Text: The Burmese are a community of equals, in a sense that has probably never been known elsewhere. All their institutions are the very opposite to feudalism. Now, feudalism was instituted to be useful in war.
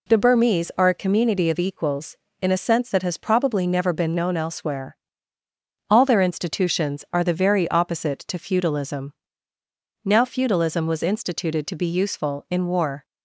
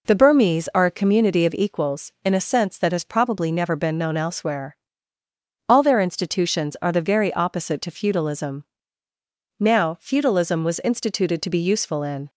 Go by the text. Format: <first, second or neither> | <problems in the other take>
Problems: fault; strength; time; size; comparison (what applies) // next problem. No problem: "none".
first | stops before "war"; at 12.2 s